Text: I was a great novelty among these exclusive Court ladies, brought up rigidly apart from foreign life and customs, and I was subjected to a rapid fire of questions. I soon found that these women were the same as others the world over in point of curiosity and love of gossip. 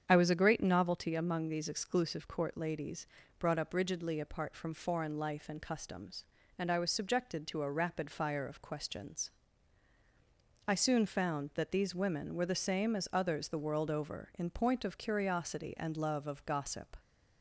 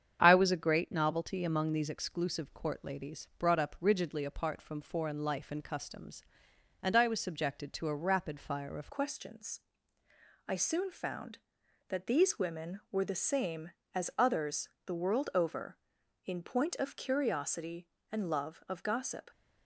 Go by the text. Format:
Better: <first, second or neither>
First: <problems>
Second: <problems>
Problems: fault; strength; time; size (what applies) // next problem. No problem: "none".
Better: first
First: starts louder than the rest; strong; until 1.0 s; 8 dB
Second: starts louder than the rest; strong; until 1.2 s; 8 dB // changes voice at "questions"; from 8.9 s on; 10.4 s long // pauses between "others" and "the"; slight; at 14.6 s; 0.18 s long